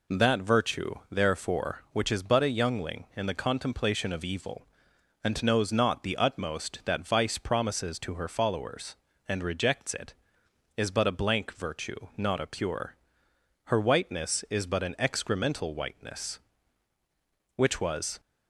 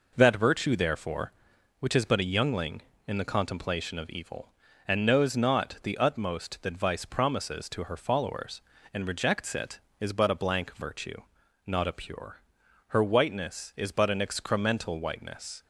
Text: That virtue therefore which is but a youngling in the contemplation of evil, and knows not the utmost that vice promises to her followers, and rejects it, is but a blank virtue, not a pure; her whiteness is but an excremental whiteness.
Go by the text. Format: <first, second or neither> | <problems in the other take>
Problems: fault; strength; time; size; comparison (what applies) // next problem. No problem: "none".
second | goes on to say "Which was"; noticeable; from 17.5 s on; 0.64 s long